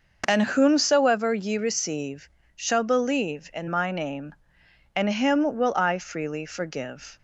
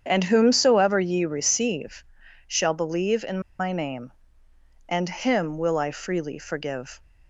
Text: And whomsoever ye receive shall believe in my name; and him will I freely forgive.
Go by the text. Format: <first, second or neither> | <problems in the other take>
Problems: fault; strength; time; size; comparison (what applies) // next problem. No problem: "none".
first | starts louder than the rest; strong; until 1.0 s; 8 dB // pauses between "receive" and "shall"; at 2.0 s; 0.42 s long; slight in the first // pauses between "in" and "my"; slight; at 3.4 s; 0.18 s long